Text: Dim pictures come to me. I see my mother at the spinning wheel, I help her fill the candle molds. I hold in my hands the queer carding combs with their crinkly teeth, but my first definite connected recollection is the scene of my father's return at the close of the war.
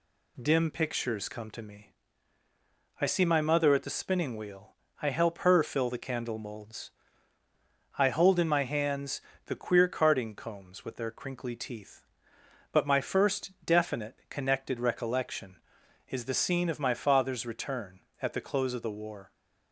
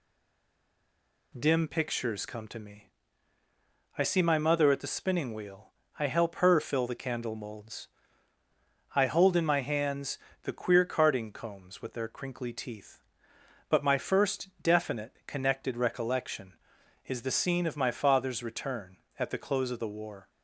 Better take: first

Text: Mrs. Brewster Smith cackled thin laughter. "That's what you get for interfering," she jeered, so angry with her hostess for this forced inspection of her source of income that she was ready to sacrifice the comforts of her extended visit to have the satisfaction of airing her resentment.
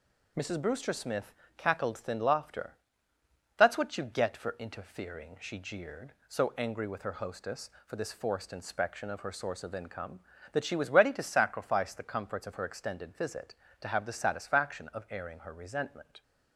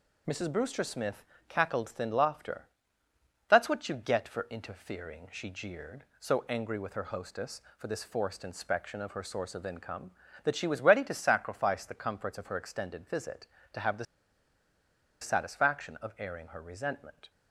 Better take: first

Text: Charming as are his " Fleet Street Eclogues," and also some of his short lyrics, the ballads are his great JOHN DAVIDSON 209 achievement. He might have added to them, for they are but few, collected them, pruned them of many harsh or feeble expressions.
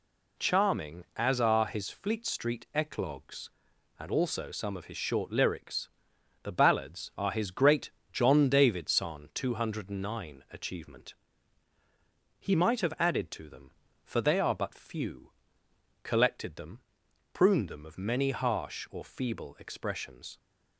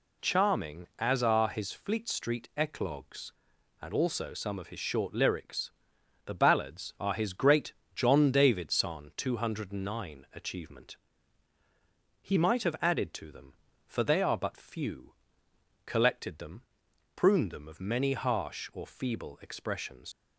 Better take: first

